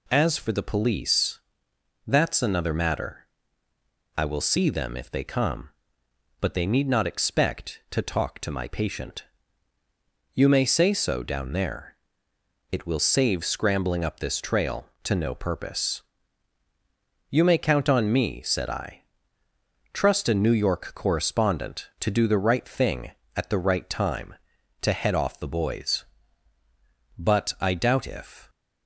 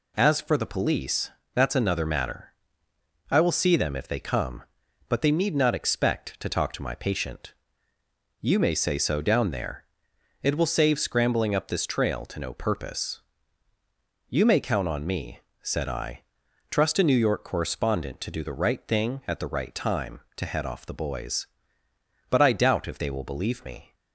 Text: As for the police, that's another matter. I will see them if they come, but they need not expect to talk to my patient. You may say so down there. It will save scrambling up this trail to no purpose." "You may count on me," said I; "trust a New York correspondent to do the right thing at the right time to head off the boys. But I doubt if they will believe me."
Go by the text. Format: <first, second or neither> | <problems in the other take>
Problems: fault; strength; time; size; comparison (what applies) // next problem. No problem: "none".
second | stops before "they will believe me"; at 28.4 s